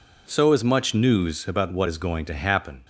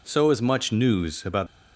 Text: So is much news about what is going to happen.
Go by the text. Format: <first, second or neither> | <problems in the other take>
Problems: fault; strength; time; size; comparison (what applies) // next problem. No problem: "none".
first | stops before "what is going to happen"; at 1.4 s